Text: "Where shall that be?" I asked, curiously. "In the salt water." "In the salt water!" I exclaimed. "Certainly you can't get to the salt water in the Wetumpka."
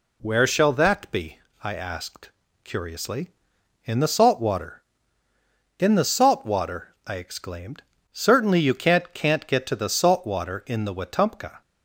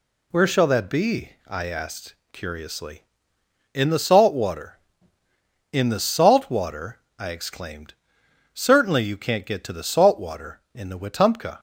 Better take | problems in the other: second | says "can't" twice; at 9.1 s

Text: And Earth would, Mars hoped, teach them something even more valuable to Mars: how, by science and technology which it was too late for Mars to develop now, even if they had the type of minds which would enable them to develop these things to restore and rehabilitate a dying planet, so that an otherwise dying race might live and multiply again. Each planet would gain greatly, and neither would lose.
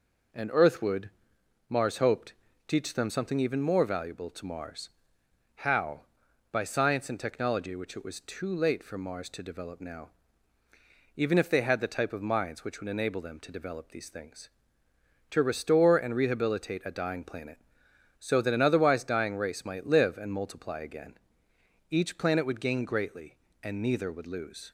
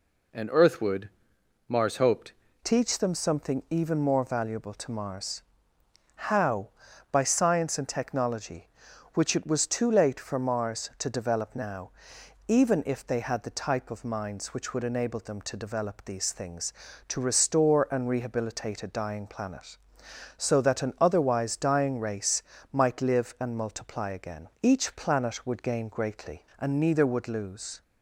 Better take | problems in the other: first | changes voice at "teach"; from 2.6 s on; 25.2 s long // pauses between "race" and "might"; slight; at 22.4 s; 0.30 s long

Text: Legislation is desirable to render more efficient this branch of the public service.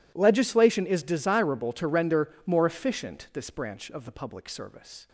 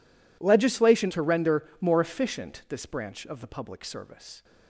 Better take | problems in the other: first | skips "is desirable"; at 1.1 s

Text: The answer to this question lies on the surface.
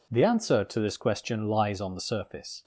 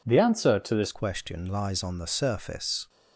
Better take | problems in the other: first | changes voice at "question"; from 0.9 s on; 1.9 s long

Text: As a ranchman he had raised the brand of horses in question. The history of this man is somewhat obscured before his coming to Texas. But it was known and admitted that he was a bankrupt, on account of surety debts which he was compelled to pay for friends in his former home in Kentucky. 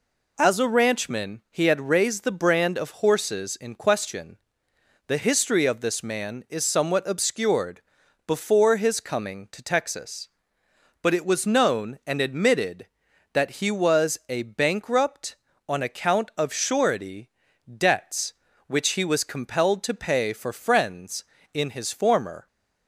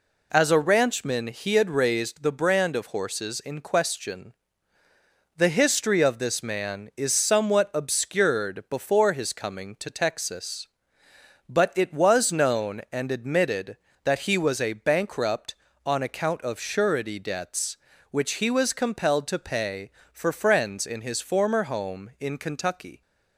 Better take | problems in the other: second | pauses between "obscured" and "before"; noticeable; at 7.8 s; 0.46 s long // pauses between "surety" and "debts"; slight; at 17.3 s; 0.34 s long // stops before "home in Kentucky"; at 22.4 s

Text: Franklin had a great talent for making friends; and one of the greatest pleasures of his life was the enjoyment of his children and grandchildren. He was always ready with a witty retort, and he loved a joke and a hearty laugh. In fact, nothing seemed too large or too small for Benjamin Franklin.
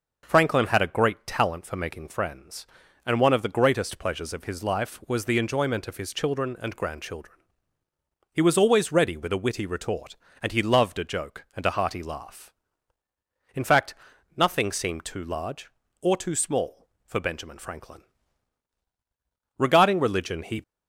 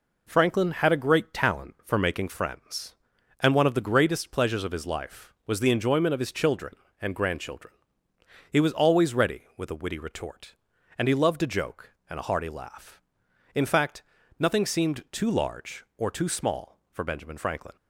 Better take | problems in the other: second | goes on to say "Regarding religion he"; noticeable; from 19.5 s on; 1.0 s long

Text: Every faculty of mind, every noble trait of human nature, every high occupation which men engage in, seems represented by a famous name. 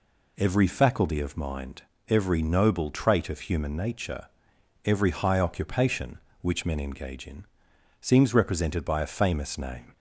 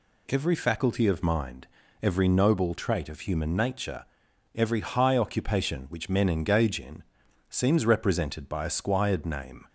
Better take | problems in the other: first | says "squired" for "famous"; at 8.7 s

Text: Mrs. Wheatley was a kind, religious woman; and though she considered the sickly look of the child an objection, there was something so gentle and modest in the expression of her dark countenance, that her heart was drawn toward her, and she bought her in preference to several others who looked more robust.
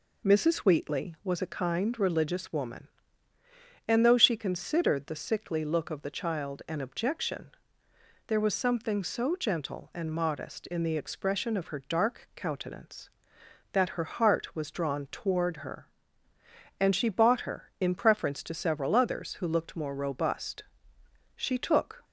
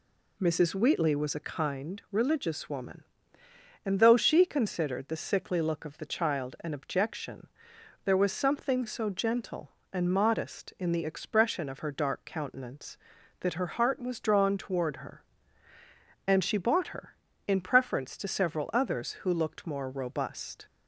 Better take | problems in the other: second | goes on to say "She took"; noticeable; from 21.3 s on; 0.68 s long

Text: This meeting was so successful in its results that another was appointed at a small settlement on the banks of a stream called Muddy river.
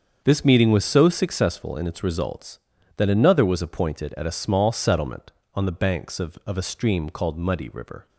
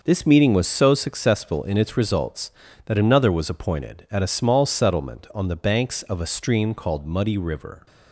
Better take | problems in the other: second | starts louder than the rest; until 1.2 s; 7 dB // says "of" twice; at 6.4 s

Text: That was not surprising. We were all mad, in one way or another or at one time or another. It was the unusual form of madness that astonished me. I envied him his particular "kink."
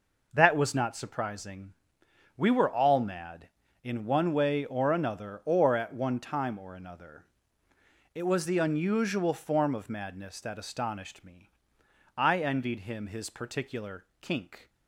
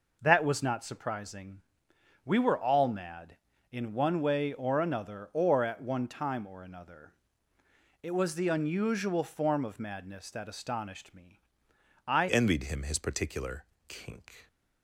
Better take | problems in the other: first | changes voice at "envied"; from 12.2 s on; 2.2 s long // pauses between "particular" and "kink"; slight; at 13.6 s; 0.22 s long; slight in the first

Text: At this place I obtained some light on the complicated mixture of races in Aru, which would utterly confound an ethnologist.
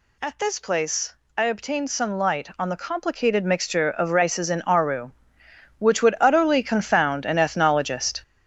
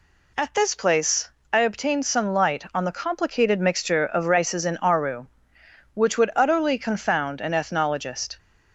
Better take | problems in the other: second | gets louder; throughout; 7 dB // pauses between "place" and "I"; slight; at 1.1 s; 0.22 s long; slight in the second

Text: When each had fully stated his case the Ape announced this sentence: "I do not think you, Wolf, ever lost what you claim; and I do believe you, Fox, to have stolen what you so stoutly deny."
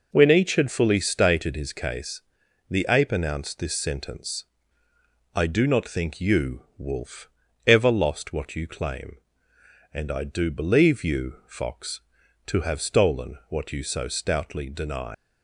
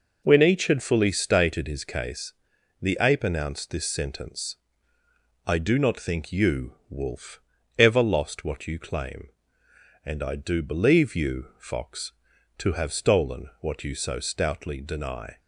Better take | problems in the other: second | pauses between "case" and "the"; noticeable; at 2.2 s; 0.50 s long; noticeable in the second // leaves "deny" unfinished; at 15.1 s; 135 ms

